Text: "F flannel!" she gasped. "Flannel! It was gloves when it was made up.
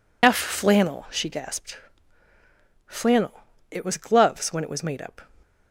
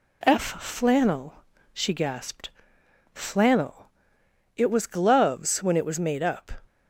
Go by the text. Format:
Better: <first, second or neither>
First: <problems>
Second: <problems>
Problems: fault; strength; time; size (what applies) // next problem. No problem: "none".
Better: second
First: loses the start of "F"; at 0.2 s; 45 ms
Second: none